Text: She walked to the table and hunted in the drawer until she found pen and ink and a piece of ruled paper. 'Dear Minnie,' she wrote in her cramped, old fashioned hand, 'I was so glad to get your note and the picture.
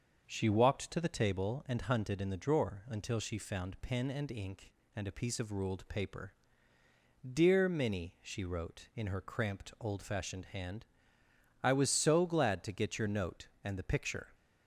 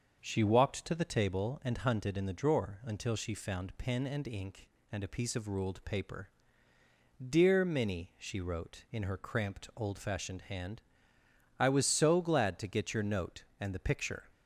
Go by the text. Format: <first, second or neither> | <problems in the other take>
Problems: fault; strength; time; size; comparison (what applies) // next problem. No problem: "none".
neither | starts louder than the rest; the same in both